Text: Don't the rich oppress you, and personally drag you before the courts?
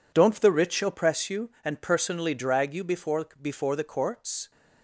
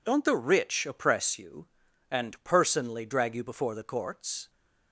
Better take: second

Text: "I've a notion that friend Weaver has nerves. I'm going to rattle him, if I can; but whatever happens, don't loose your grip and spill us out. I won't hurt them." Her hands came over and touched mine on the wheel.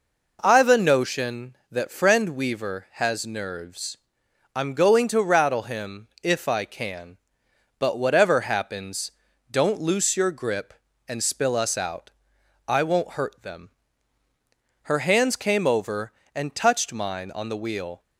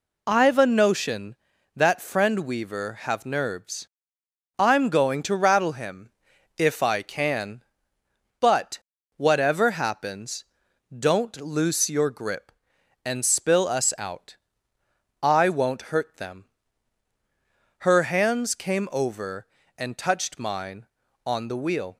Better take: first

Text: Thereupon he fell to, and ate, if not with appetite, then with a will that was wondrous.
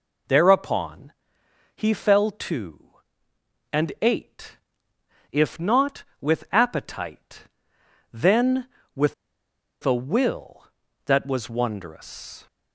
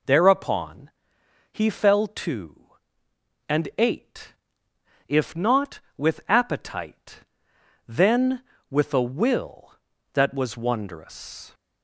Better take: second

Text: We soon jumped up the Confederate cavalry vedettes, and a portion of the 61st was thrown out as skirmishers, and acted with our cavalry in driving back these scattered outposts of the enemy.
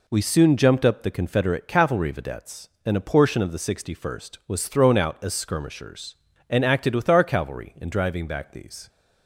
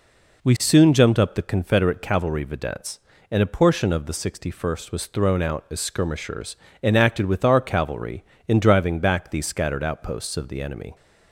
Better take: second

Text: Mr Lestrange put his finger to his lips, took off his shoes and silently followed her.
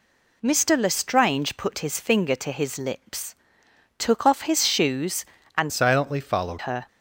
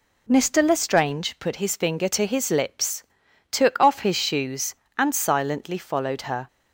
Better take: second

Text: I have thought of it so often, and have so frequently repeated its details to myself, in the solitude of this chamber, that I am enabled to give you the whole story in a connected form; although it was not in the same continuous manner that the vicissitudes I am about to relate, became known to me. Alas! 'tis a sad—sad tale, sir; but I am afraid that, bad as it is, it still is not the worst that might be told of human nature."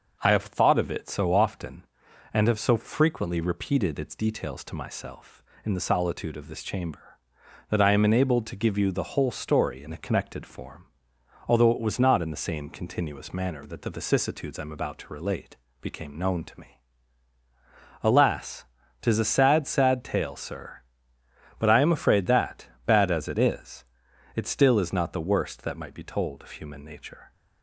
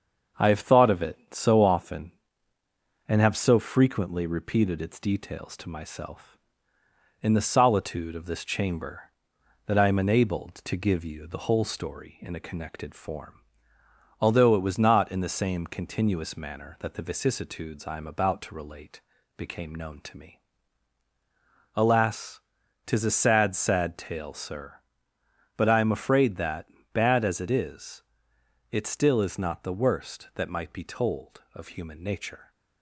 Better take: first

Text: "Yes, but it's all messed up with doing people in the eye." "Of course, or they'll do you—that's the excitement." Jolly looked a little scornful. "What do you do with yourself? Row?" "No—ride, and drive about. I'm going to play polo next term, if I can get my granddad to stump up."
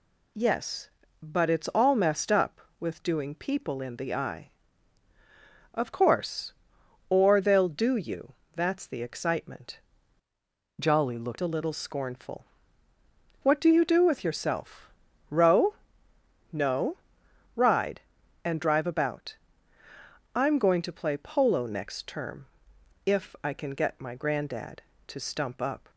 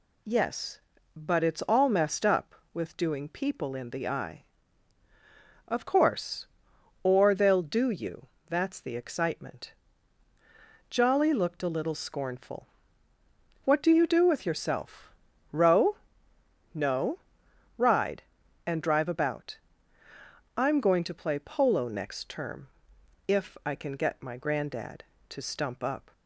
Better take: second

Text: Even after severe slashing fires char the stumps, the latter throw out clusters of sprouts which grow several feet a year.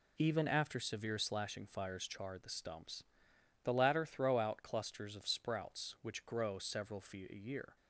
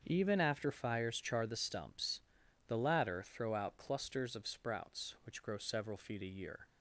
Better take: first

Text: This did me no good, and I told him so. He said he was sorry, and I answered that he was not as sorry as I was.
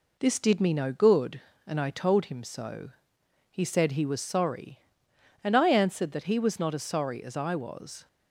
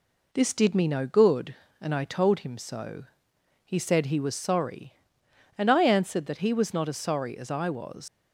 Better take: first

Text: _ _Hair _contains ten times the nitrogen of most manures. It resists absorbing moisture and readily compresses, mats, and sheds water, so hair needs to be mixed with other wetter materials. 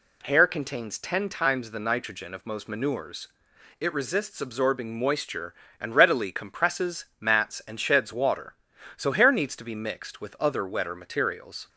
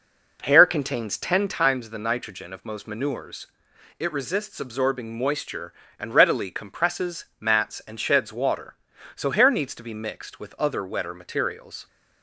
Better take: first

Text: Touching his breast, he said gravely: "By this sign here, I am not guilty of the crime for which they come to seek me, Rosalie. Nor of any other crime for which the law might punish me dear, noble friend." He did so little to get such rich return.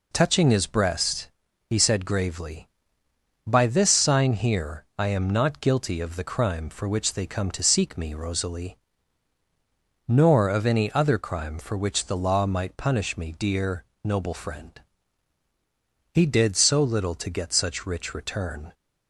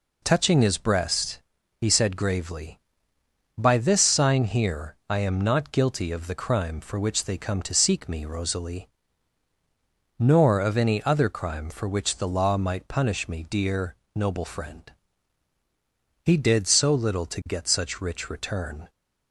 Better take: neither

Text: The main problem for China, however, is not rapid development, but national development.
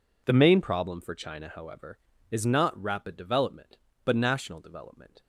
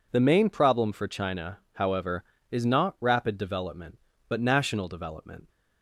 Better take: neither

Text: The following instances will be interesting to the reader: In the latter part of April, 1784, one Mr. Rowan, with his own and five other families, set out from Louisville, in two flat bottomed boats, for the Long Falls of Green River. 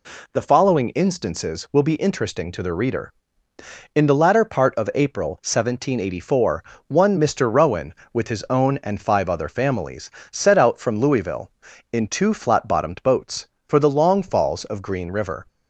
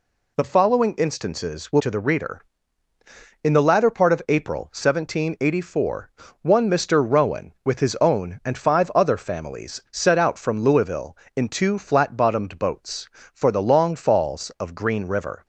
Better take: first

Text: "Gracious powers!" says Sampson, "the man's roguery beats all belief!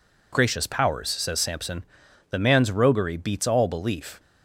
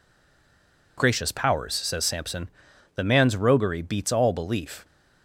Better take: first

